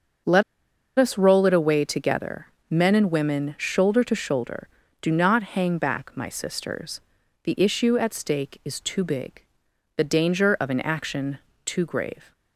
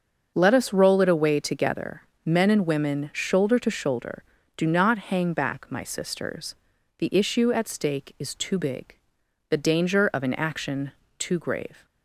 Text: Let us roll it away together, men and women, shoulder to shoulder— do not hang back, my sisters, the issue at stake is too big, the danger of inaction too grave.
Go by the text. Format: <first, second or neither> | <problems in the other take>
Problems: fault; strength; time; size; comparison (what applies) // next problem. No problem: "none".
second | starts louder than the rest; until 1.8 s; 6.5 dB; also in the second // pauses between "Let" and "us"; noticeable; at 0.4 s; 0.56 s long // pauses between "inaction" and "too"; slight; at 11.3 s; 0.26 s long; slight in the second